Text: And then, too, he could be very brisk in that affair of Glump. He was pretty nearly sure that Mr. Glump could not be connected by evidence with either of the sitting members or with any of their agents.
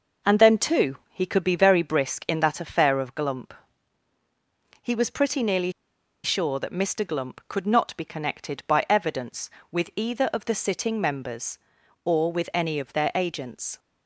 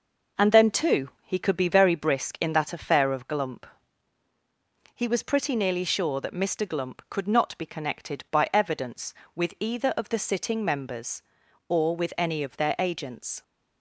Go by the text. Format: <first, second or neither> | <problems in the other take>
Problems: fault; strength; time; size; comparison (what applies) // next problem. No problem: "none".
second | pauses between "nearly" and "sure"; noticeable; at 5.7 s; 0.52 s long